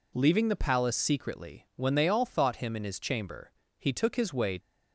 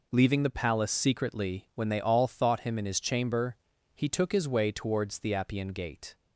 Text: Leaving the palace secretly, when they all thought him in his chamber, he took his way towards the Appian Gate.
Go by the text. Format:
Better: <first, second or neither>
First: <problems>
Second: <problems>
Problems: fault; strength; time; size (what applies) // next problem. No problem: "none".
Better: second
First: stops before "towards the Appian Gate"; at 4.5 s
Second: none